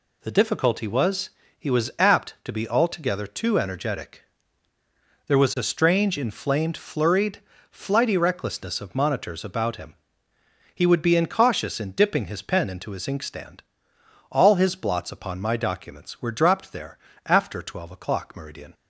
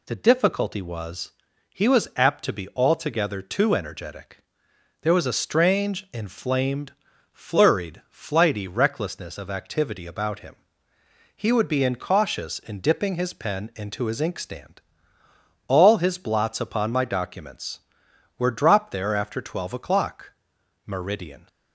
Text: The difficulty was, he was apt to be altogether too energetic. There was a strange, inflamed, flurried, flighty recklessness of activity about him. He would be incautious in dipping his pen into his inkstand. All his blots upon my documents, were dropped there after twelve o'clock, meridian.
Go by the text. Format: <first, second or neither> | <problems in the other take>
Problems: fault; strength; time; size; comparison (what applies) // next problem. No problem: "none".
second | says "monitors" for "activity"; at 8.9 s // pauses between "there" and "after"; slight; at 16.9 s; 0.28 s long